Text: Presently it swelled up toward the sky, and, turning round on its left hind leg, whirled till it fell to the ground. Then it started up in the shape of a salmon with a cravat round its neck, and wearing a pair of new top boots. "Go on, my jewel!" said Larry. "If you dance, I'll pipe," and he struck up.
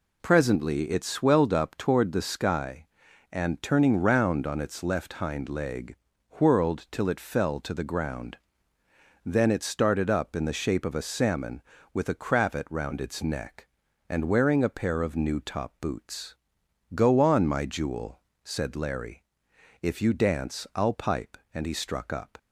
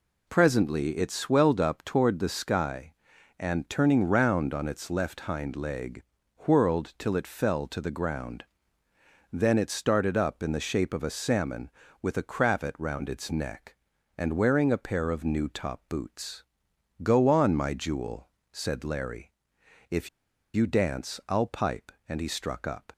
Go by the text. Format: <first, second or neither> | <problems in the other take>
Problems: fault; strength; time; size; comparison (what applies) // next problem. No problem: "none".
first | pauses between "If" and "you"; at 20.0 s; 0.45 s long